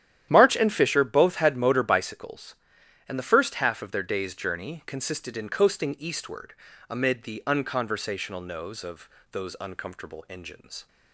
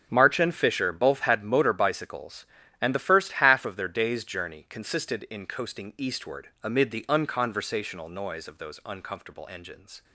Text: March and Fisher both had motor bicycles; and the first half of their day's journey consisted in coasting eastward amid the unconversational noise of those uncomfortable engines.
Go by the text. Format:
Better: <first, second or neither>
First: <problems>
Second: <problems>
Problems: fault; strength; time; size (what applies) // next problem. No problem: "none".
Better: second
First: starts louder than the rest; strong; until 1.3 s; 11 dB // pauses between "eastward" and "amid"; at 6.5 s; 0.38 s long // says "nose" for "noise"; at 8.4 s // pauses between "of" and "those"; slight; at 9.0 s; 0.24 s long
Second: starts louder than the rest; until 1.1 s; 6.5 dB // pauses between "eastward" and "amid"; slight; at 6.4 s; 0.16 s long